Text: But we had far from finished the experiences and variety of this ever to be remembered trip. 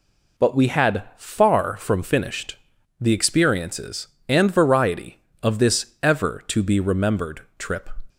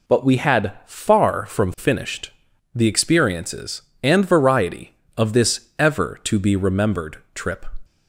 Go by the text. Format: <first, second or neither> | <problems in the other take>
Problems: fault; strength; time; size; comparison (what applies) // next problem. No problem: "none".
neither | pauses between "finished" and "the"; the same in both // pauses between "remembered" and "trip"; slight; the same in both